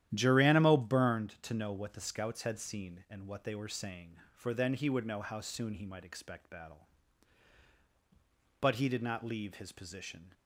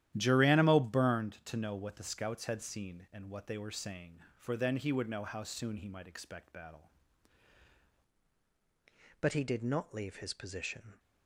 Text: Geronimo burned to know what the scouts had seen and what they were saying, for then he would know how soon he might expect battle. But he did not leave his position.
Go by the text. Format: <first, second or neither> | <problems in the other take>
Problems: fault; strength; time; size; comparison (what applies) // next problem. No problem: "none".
first | starts louder than the rest; strong; until 1.1 s; 12 dB; strong in the first // changes voice at "But"; from 9.2 s on; 1.7 s long